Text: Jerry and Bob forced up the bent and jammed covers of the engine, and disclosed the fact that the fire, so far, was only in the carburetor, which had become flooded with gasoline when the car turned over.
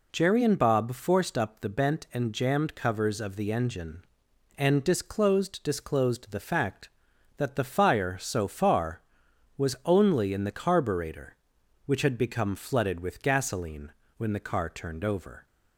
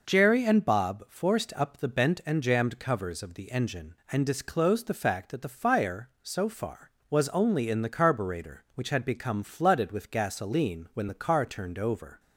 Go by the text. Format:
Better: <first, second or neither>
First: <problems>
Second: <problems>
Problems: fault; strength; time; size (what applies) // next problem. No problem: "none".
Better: second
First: says "disclosed" twice; at 5.6 s // pauses between "gasoline" and "when"; slight; at 13.9 s; 0.26 s long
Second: none